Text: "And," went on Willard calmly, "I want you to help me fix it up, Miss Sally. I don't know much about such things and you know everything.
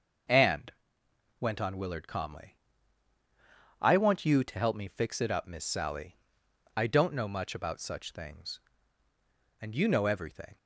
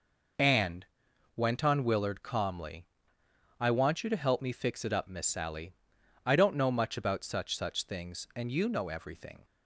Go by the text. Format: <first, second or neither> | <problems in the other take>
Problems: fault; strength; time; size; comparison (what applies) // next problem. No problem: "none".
first | says "such" twice; at 7.5 s